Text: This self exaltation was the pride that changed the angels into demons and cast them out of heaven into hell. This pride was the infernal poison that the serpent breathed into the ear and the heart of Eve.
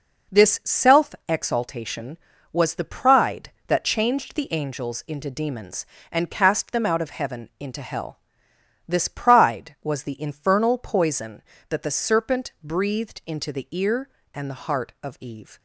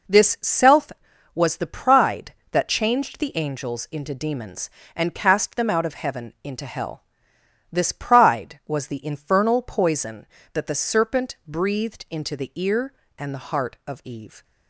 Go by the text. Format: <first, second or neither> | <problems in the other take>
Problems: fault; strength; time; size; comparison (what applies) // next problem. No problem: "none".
first | skips "exaltation"; at 1.1 s